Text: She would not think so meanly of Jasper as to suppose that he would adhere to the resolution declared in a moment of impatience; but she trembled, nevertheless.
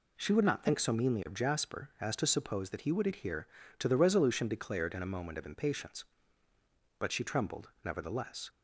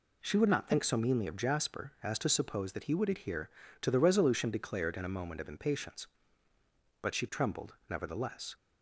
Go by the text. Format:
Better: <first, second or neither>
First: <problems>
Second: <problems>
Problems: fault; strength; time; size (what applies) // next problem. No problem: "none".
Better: neither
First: none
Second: none